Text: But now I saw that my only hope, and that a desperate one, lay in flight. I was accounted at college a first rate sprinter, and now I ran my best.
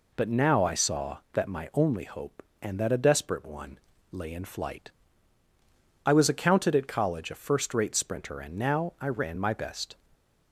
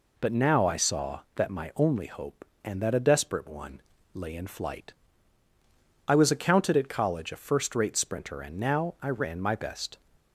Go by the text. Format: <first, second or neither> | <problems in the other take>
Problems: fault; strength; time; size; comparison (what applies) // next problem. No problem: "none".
neither | none